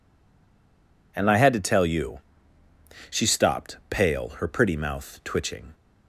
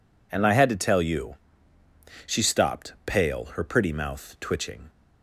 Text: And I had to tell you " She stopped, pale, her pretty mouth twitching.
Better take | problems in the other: second | stays silent before the first word; until 1.1 s; 1.1 s long

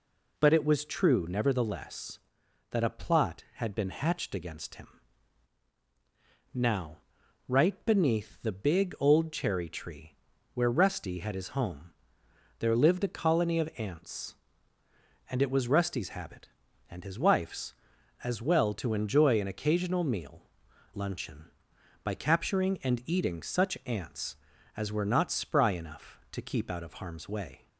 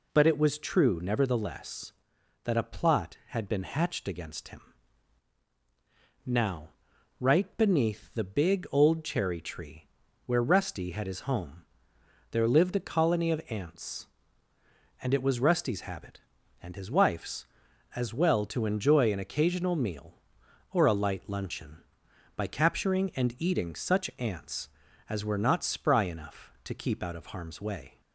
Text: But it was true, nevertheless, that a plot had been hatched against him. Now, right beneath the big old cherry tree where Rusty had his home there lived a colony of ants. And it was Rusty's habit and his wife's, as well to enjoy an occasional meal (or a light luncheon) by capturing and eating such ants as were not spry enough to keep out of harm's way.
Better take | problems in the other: second | pauses between "tree" and "where"; at 10.1 s; 0.38 s long; also in the second // pauses between "home" and "there"; noticeable; at 11.9 s; 0.66 s long; noticeable in the second // skips "or a light"; at 20.7 s

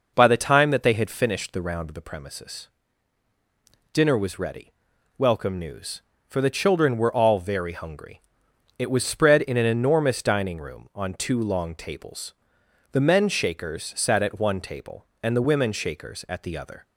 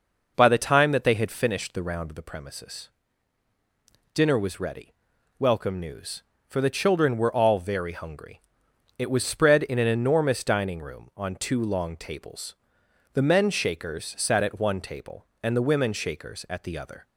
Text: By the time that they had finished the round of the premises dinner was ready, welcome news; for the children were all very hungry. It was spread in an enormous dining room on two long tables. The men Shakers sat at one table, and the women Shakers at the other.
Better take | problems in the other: neither | pauses between "premises" and "dinner"; the same in both

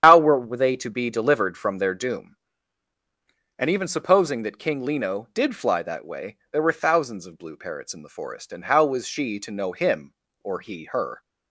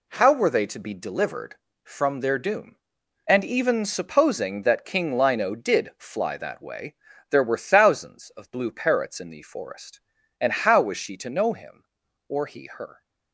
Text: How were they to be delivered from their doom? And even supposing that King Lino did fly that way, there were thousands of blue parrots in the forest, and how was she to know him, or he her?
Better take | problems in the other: second | loses the start of "How"; at 0.0 s; 90 ms // starts louder than the rest; strong; until 1.0 s; 9.5 dB

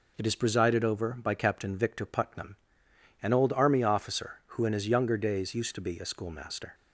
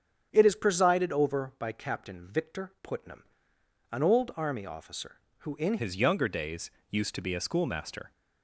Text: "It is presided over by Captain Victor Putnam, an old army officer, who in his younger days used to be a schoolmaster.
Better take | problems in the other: first | starts louder than the rest; strong; until 1.3 s; 8 dB // changes voice at "his"; from 5.7 s on; 2.4 s long // pauses between "days" and "used"; slight; at 6.6 s; 0.20 s long

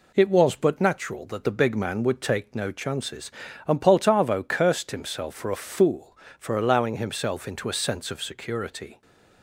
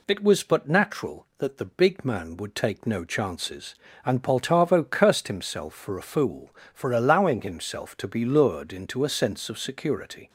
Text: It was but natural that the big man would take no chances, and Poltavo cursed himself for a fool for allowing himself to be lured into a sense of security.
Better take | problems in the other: second | skips "to be lured"; at 7.4 s

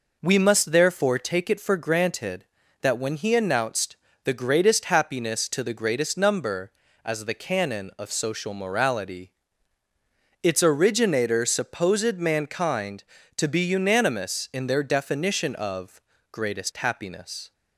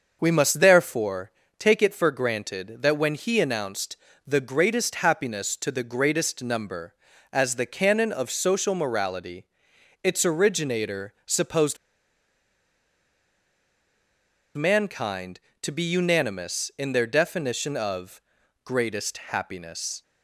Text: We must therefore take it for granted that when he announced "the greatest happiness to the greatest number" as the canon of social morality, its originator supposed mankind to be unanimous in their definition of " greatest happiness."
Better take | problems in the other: first | starts louder than the rest; noticeable; until 1.2 s; 6 dB // pauses between "therefore" and "take"; slight; at 1.3 s; 0.26 s long // pauses between "announced" and "the"; slight; at 3.9 s; 0.30 s long; slight in the first // pauses between "supposed" and "mankind"; strong; at 11.7 s; 2.7 s long

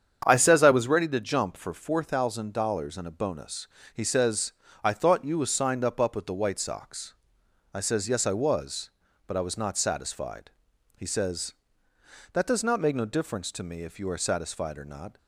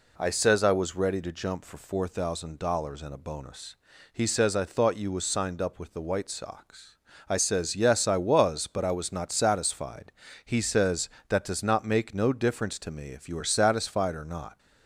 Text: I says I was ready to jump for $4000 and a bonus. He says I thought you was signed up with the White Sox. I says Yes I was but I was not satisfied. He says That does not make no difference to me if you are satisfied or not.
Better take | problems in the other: second | starts louder than the rest; strong; until 1.2 s; 8 dB // pauses between "says" and "I"; slight; at 4.5 s; 0.30 s long // says "up" twice; at 5.9 s

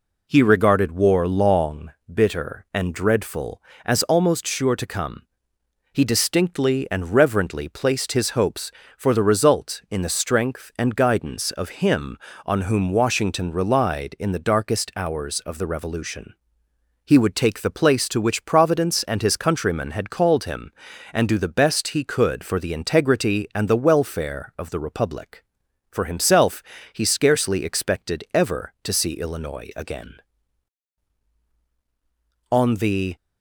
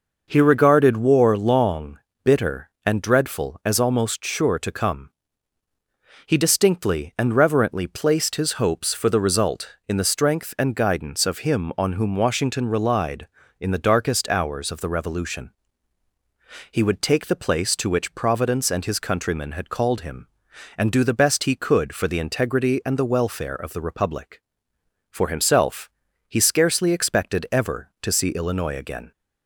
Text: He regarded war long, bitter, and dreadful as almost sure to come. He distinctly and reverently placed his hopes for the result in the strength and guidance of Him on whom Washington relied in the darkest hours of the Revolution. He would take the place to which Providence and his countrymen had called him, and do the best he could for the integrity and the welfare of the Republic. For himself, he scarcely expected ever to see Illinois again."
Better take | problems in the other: second | goes on to say "On the"; noticeable; from 32.5 s on; 0.64 s long

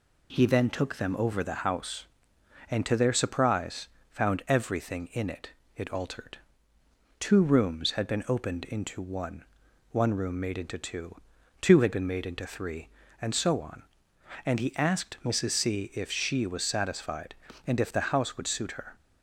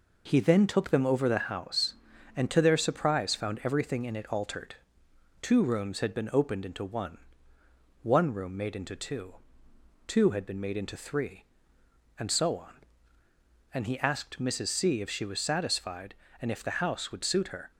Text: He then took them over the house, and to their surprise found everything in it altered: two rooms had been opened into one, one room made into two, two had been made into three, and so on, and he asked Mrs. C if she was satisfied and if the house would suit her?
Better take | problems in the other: second | pauses between "surprise" and "found"; slight; at 3.8 s; 0.24 s long // says "it" twice; at 5.7 s

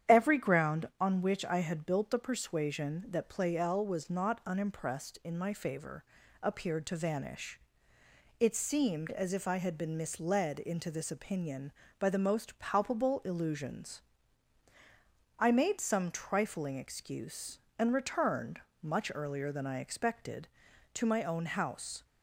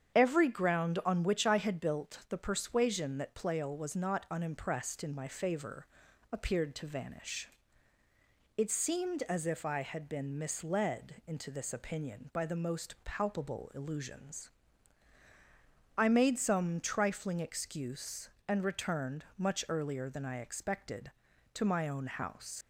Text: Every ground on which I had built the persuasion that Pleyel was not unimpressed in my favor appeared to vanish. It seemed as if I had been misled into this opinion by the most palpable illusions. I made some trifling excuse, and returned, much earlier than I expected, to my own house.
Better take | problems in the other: first | starts louder than the rest; strong; until 1.2 s; 8 dB; strong in the first // pauses between "favor" and "appeared"; noticeable; at 5.8 s; 0.46 s long; also in the first // leaves "house" unfinished; at 22.6 s; 105 ms

